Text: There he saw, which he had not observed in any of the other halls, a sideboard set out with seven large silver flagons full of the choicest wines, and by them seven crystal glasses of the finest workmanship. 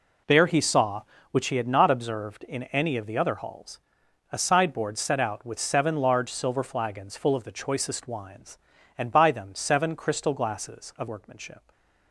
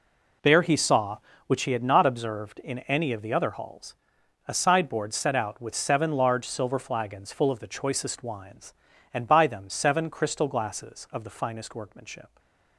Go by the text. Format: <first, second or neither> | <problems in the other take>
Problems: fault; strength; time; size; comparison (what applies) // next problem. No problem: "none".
second | skips "the finest"; at 11.0 s // stays silent after the last word; slight; from 11.5 s on; 0.6 s long; slight in the second